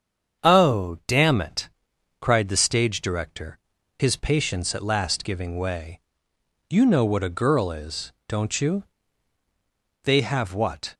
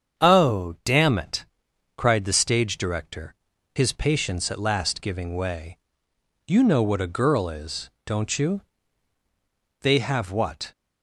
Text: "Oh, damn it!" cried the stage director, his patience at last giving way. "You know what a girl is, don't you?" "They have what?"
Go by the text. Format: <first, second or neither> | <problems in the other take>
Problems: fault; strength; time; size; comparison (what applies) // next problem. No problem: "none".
neither | starts louder than the rest; strong; the same in both